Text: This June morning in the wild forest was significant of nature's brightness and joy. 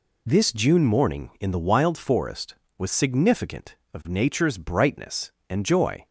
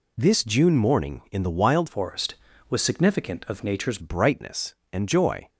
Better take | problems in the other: first | changes voice from "forest" to "nature's"; from 1.8 to 3.9 s; 2.1 s long

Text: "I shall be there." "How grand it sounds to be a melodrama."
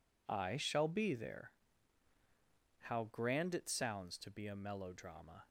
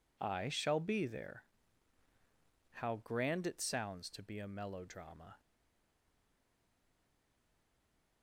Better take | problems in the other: first | stays silent after the last word; strong; from 5.3 s on; 2.9 s long

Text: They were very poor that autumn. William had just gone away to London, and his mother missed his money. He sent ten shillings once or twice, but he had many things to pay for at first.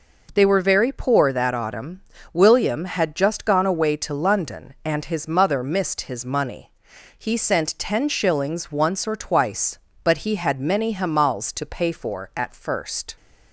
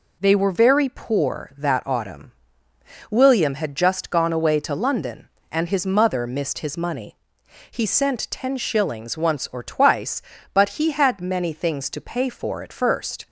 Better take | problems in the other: second | says "hamals" for "things"; at 10.9 s

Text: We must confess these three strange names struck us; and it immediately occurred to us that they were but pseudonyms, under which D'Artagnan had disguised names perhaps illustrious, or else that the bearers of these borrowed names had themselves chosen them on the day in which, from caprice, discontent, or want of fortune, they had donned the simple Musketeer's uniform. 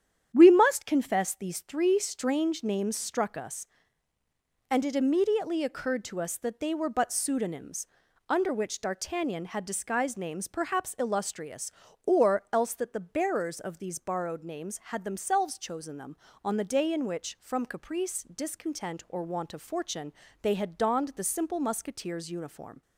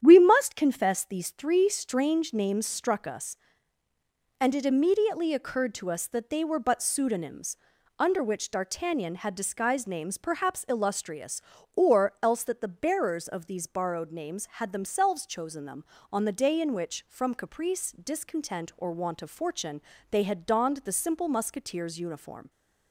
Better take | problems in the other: neither | starts louder than the rest; strong; the same in both

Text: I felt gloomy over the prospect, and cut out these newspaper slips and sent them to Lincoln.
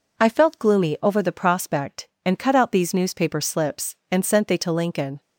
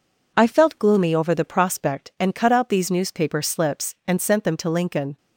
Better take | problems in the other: second | says "they" for "them"; at 4.4 s

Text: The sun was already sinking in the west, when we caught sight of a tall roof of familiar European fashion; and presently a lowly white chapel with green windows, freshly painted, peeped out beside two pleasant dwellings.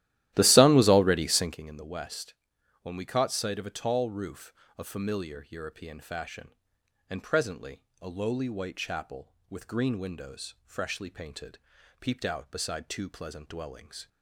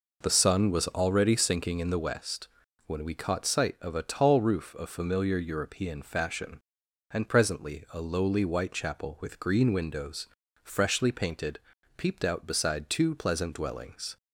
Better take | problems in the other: second | starts louder than the rest; strong; until 1.6 s; 14 dB // pauses between "presently" and "a"; slight; at 7.8 s; 0.16 s long

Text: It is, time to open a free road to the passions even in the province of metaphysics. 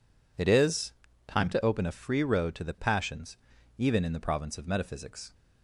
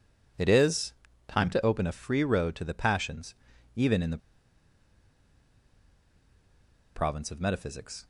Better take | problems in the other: first | pauses between "passions" and "even"; at 3.3 s; 0.40 s long; also in the first // pauses between "the" and "province"; strong; at 4.1 s; 2.7 s long

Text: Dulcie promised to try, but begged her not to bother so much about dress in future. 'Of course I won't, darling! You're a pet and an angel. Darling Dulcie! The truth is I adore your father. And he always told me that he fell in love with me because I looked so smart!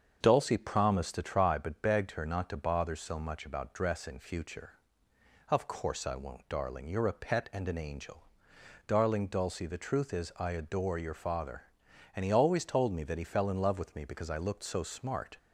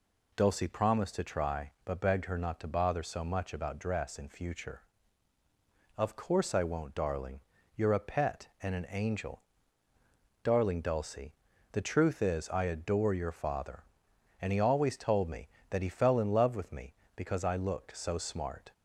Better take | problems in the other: second | starts louder than the rest; until 1.6 s; 7 dB

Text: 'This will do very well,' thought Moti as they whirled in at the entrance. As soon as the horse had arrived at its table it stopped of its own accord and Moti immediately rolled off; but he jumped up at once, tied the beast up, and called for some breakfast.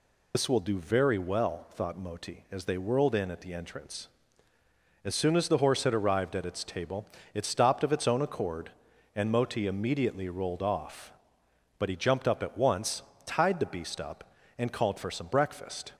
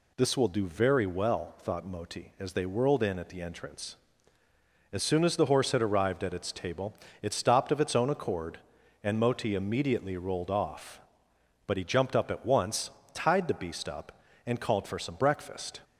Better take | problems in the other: second | loses the start of "This"; at 0.3 s; 75 ms // pauses between "table" and "it"; slight; at 7.0 s; 0.30 s long; slight in the second

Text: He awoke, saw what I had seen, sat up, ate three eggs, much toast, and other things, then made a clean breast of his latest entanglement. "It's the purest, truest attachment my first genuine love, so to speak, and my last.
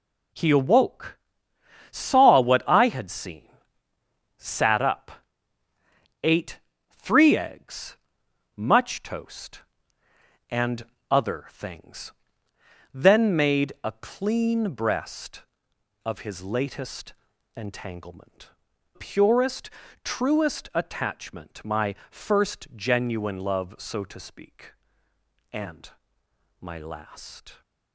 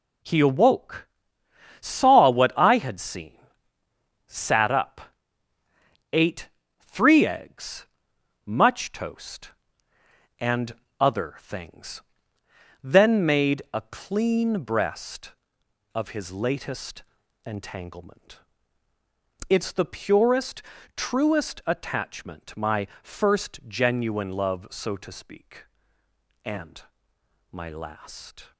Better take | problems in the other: second | pauses between "ate" and "three"; slight; at 6.5 s; 0.32 s long; slight in the second // pauses between "and" and "other"; slight; at 10.8 s; 0.26 s long; slight in the second // pauses between "latest" and "entanglement"; at 17.1 s; 0.42 s long; also in the second // skips "It's the"; at 18.7 s // pauses between "and" and "my"; noticeable; at 25.8 s; 0.70 s long; noticeable in the second

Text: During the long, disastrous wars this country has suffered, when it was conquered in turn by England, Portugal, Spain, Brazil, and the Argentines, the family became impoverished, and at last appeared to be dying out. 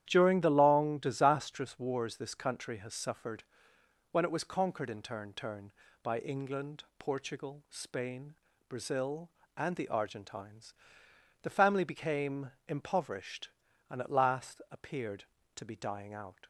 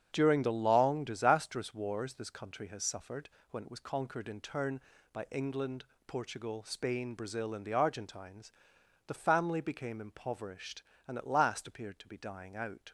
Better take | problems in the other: second | starts louder than the rest; strong; until 1.0 s; 11 dB; strong in the second // says "turn" twice; at 5.3 s // pauses between "became" and "impoverished"; slight; at 12.5 s; 0.18 s long

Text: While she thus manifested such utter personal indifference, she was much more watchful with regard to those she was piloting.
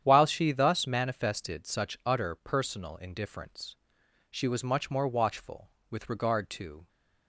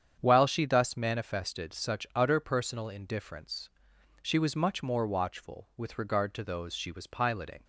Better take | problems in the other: second | starts louder than the rest; strong; until 1.0 s; 9.5 dB; strong in the second // stops before "those she was piloting"; at 6.8 s

